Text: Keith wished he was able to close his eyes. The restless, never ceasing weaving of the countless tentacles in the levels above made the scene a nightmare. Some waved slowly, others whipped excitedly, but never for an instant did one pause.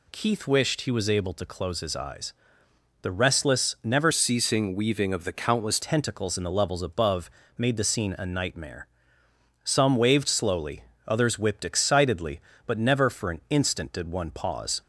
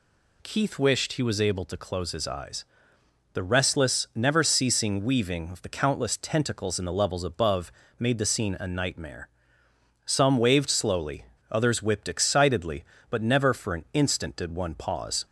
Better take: second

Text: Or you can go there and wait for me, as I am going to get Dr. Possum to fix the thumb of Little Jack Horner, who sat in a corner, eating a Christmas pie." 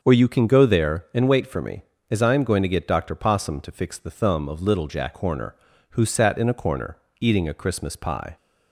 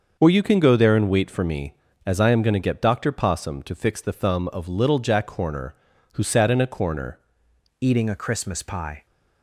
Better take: first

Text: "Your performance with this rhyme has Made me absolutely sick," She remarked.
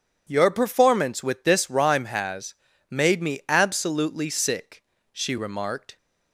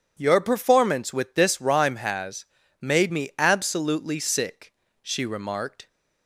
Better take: neither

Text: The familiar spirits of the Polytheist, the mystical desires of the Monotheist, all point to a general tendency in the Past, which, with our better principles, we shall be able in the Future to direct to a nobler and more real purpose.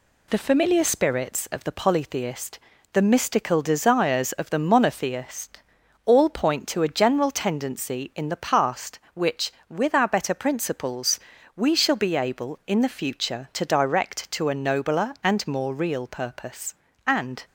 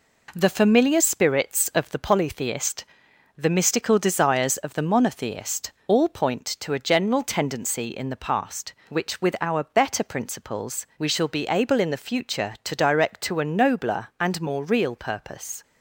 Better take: second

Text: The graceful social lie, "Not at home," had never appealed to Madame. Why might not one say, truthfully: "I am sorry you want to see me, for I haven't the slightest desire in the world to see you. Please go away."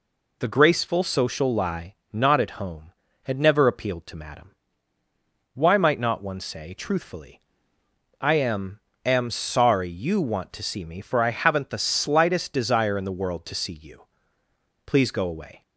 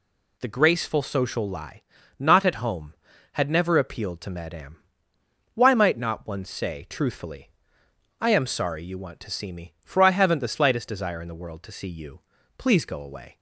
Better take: second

